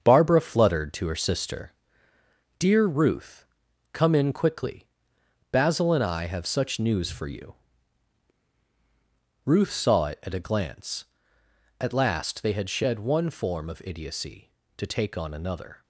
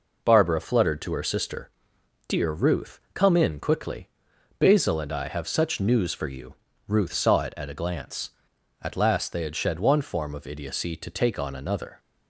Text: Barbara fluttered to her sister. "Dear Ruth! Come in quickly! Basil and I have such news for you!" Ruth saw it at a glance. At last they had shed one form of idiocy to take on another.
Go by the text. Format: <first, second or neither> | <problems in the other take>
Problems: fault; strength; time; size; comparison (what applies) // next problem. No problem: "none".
second | gets quieter; throughout; 6.5 dB